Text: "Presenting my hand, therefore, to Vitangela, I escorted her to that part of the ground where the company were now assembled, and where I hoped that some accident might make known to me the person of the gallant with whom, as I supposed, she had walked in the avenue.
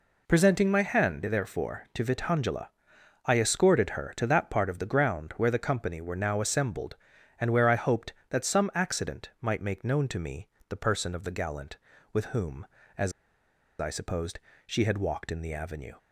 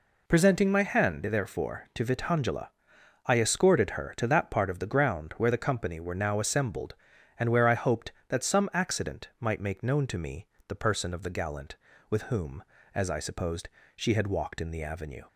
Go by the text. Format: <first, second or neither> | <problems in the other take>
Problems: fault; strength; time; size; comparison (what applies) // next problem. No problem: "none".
second | pauses between "me" and "the"; slight; at 10.4 s; 0.22 s long; slight in the second // pauses between "as" and "I"; noticeable; at 13.1 s; 0.68 s long